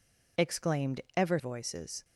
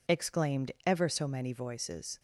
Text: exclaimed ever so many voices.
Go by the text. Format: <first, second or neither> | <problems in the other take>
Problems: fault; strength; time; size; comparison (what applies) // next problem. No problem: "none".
second | skips "so many"; at 1.3 s